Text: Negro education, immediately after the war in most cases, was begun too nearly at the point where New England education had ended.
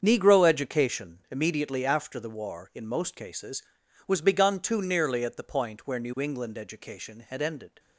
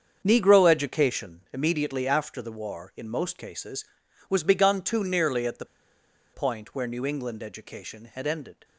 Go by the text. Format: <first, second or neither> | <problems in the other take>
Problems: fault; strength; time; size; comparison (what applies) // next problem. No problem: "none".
first | starts louder than the rest; strong; until 1.2 s; 7.5 dB; strong in the first // pauses between "the" and "point"; noticeable; at 5.6 s; 0.68 s long